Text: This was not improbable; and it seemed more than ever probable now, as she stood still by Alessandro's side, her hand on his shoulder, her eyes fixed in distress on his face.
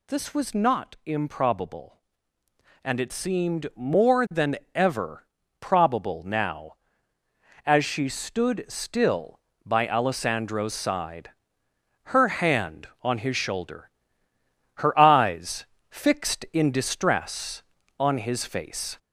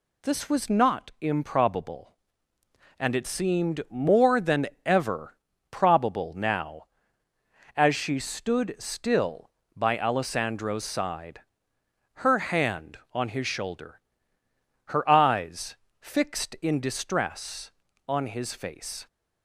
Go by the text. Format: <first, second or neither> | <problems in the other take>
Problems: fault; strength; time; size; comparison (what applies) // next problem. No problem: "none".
second | gets louder; slight; throughout; 2.5 dB // pauses between "than" and "ever"; slight; at 4.5 s; 0.18 s long; slight in the second // pauses between "ever" and "probable"; slight; at 5.2 s; 0.36 s long; slight in the second // pauses between "eyes" and "fixed"; slight; at 15.6 s; 0.28 s long; slight in the second